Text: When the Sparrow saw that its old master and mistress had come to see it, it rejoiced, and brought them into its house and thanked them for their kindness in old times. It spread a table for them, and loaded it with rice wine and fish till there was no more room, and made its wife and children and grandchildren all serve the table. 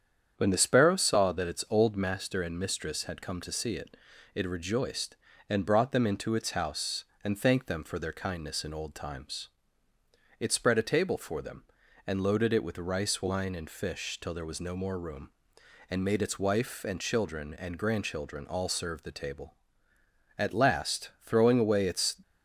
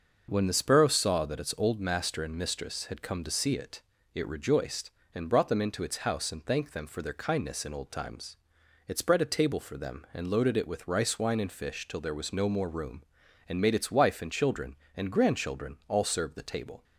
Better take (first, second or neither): second